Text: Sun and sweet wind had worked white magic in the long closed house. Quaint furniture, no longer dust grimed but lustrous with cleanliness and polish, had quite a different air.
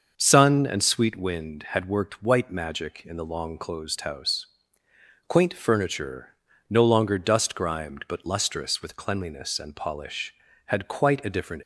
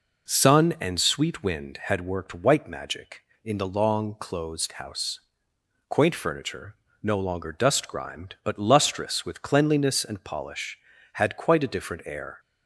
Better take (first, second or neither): second